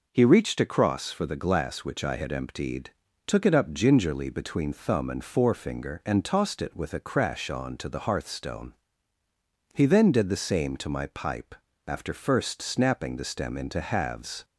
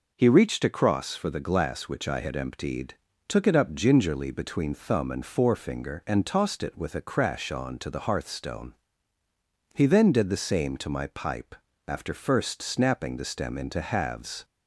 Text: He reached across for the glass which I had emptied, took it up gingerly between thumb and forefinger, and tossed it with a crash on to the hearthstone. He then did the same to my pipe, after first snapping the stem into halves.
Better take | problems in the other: neither | none

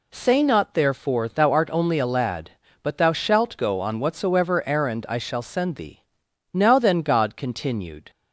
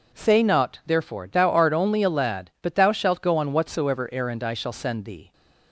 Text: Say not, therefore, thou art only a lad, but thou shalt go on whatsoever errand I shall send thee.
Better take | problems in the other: second | goes on to say "Now then God continued"; from 6.5 s on; 1.5 s long

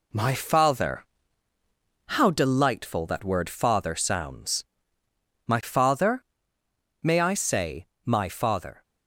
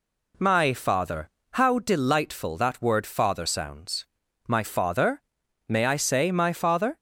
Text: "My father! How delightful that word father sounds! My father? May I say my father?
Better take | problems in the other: second | gets quieter; noticeable; throughout; 5 dB // pauses between "say" and "my"; slight; at 7.8 s; 0.18 s long

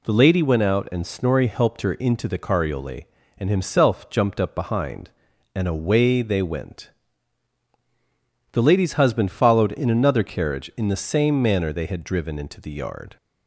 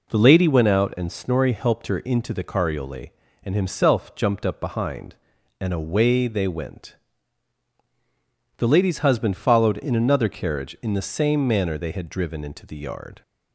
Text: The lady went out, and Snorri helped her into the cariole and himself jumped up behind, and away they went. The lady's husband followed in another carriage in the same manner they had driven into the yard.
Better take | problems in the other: first | starts louder than the rest; noticeable; until 1.1 s; 4.5 dB

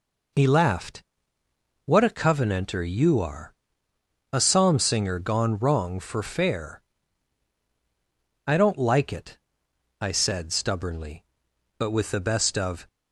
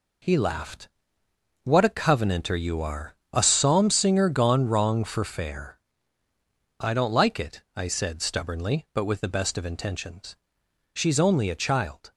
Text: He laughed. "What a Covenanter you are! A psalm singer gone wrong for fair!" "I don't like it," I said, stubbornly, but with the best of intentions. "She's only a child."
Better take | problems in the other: second | stops before "intentions She's only a child"; at 12.8 s

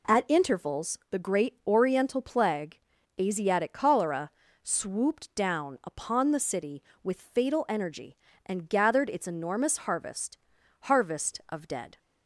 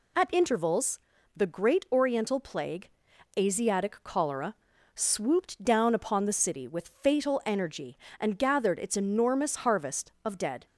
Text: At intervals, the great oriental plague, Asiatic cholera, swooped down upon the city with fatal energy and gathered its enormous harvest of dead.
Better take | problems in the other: second | says "harvest" twice; at 10.8 s

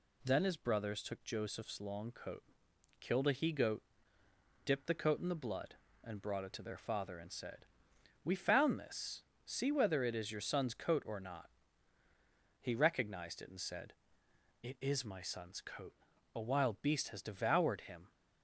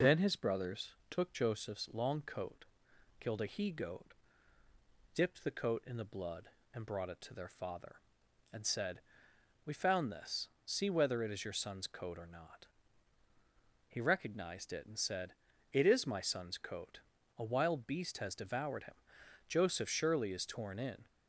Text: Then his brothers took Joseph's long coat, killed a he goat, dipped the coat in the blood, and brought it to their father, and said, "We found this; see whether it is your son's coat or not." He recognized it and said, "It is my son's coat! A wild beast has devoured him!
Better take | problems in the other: first | pauses between "brothers" and "took"; slight; at 0.9 s; 0.18 s long // goes on to say "Joseph surely is torn in"; from 19.4 s on; 1.5 s long

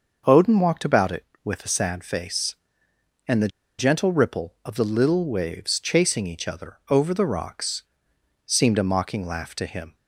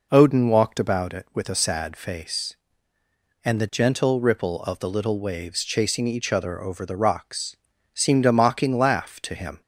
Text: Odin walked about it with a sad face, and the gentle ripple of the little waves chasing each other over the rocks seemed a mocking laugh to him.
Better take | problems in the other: second | starts louder than the rest; noticeable; until 1.4 s; 6 dB // pauses between "the" and "gentle"; slight; at 3.4 s; 0.30 s long // pauses between "rocks" and "seemed"; noticeable; at 7.8 s; 0.60 s long; also in the second

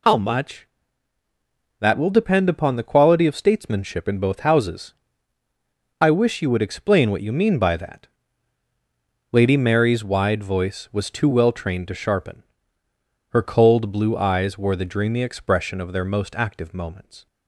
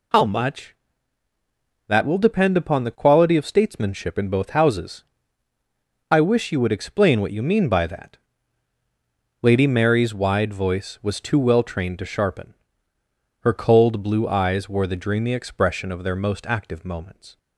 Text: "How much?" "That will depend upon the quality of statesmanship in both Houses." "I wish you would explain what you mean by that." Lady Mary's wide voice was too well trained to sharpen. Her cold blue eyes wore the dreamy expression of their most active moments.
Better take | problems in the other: neither | none

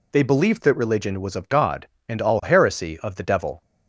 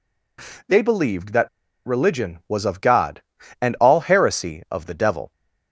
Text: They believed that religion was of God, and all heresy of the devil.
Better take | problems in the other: first | pauses between "that" and "religion"; at 1.4 s; 0.38 s long

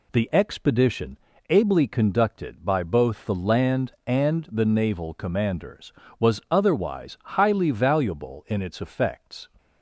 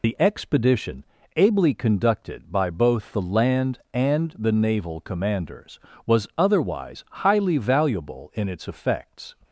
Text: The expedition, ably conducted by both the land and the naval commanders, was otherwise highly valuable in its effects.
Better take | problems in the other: first | loses the start of "The"; at 0.0 s; 65 ms

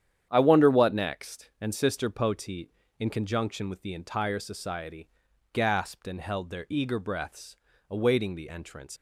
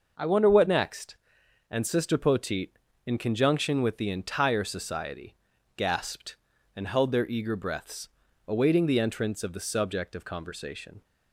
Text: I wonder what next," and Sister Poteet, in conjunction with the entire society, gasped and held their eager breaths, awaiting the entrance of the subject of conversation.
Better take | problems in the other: second | starts louder than the rest; strong; until 1.3 s; 9.5 dB // stops before "of the subject of conversation"; at 8.9 s

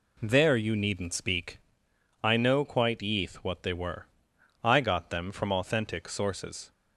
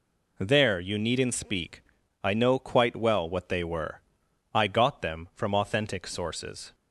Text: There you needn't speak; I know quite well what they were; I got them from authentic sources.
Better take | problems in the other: second | says "yeath" for "well"; at 2.9 s

